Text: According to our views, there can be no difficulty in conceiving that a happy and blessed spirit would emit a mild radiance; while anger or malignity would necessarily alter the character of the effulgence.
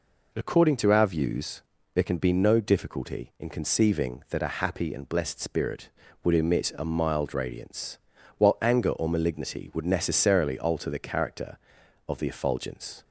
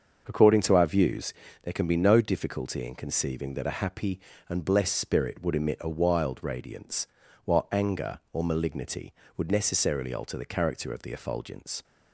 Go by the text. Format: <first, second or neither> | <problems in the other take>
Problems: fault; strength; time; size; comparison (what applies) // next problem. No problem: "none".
first | starts louder than the rest; until 1.2 s; 6.5 dB // says "wild" for "mild"; at 5.8 s